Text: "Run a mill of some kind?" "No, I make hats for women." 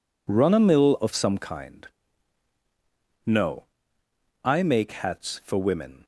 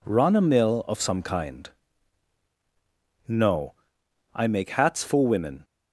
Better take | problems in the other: neither | none

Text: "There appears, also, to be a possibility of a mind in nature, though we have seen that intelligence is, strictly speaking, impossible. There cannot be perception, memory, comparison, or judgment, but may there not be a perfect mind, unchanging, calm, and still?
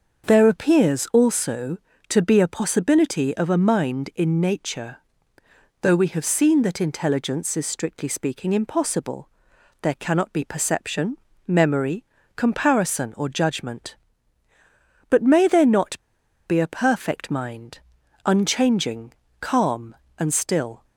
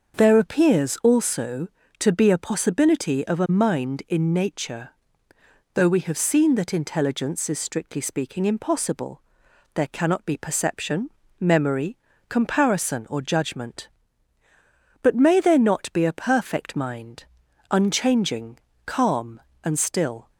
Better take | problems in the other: second | starts louder than the rest; until 1.3 s; 6.5 dB; also in the second // pauses between "not" and "be"; noticeable; at 15.9 s; 0.48 s long

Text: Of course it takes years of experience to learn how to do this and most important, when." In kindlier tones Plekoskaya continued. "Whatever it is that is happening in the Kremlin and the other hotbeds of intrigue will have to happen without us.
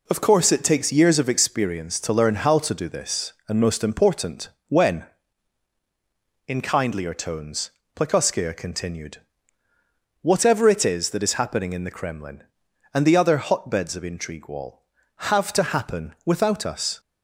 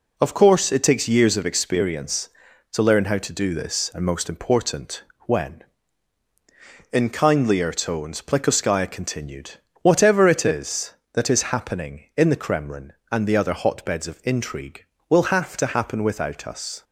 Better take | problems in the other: second | pauses between "tones" and "Plekoskaya"; slight; at 7.7 s; 0.24 s long // says "wall" for "will"; at 14.4 s

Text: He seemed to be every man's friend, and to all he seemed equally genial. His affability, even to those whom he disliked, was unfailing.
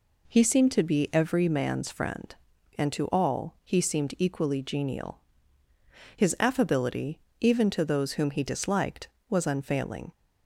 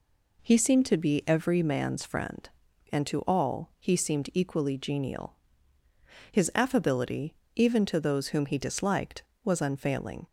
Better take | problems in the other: neither | none

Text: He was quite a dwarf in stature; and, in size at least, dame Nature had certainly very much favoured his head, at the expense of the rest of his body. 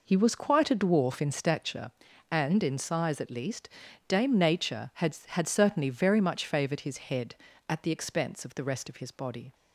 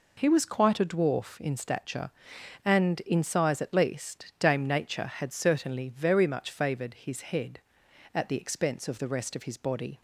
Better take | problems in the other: second | says "had" twice; at 5.2 s

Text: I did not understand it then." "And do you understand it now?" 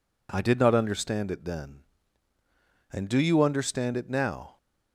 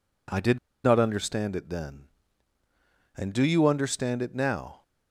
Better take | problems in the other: first | pauses between "did" and "not"; slight; at 0.5 s; 0.25 s long

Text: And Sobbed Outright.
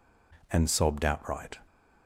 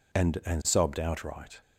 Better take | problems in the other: first | says "And" twice; at 0.4 s

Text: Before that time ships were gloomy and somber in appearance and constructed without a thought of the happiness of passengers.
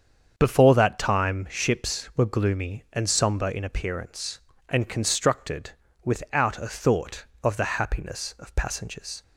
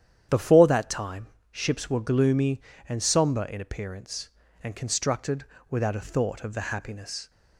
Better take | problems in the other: first | starts louder than the rest; strong; until 1.5 s; 9.5 dB; strong in the first // pauses between "time" and "ships"; slight; at 1.2 s; 0.24 s long // pauses between "constructed" and "without"; slight; at 5.4 s; 0.28 s long; slight in the first // stops before "of passengers"; at 7.2 s

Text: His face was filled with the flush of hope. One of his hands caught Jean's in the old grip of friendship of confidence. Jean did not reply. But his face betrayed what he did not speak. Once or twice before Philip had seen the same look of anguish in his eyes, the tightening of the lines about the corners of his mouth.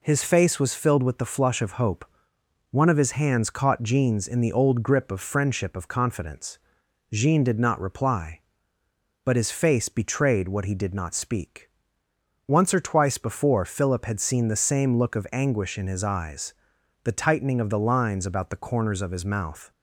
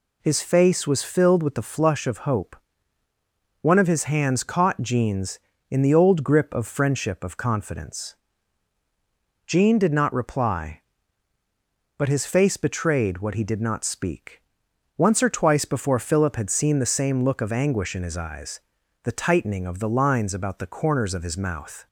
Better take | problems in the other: neither | none

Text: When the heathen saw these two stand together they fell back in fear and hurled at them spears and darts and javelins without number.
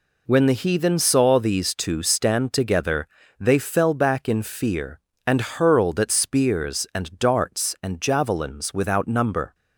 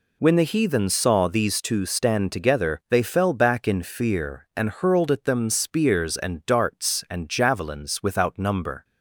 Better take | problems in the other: second | pauses between "together" and "they"; slight; at 3.0 s; 0.32 s long // skips "them"; at 6.1 s

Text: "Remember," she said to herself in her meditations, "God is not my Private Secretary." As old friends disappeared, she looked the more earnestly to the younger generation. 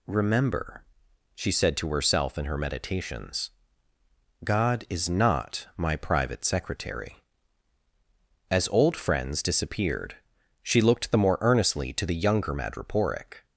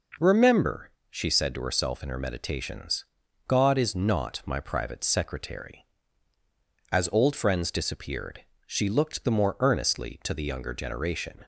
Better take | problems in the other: second | says "madreporic" for "generation"; at 12.5 s

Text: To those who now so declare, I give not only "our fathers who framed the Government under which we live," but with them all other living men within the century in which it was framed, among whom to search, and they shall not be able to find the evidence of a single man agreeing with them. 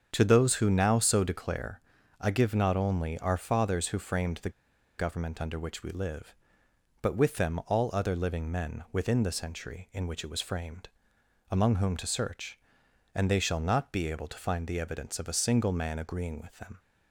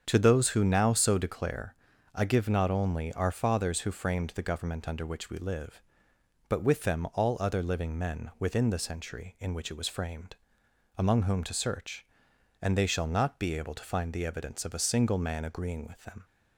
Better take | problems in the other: second | starts louder than the rest; until 1.1 s; 7 dB; strong in the second // pauses between "the" and "Government"; noticeable; at 4.4 s; 0.48 s long

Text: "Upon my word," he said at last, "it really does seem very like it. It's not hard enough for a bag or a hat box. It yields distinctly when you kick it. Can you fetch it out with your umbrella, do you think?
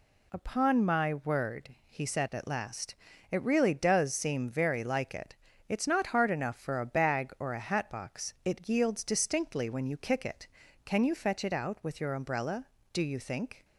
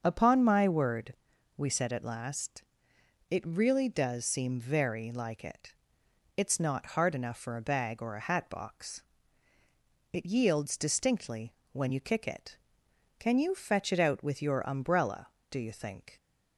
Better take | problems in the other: first | starts louder than the rest; until 1.0 s; 7 dB // says "we" for "he"; at 1.5 s // pauses between "distinctly" and "when"; slight; at 11.5 s; 0.18 s long

